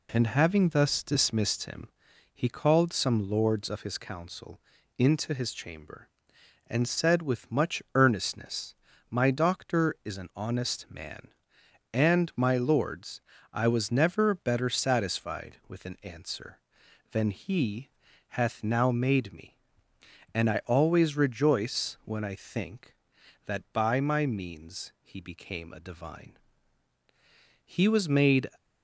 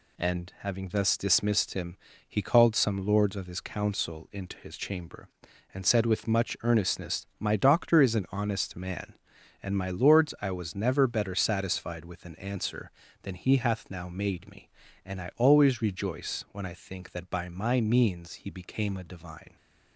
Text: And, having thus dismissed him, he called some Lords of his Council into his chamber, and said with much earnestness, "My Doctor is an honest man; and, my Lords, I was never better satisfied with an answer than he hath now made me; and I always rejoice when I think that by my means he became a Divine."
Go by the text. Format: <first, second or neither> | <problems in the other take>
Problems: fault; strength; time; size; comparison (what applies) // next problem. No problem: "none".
second | pauses between "Council" and "into"; at 4.6 s; 0.38 s long // pauses between "he" and "hath"; at 17.8 s; 0.42 s long // goes on to say "He was made"; noticeable; from 27.6 s on; 0.86 s long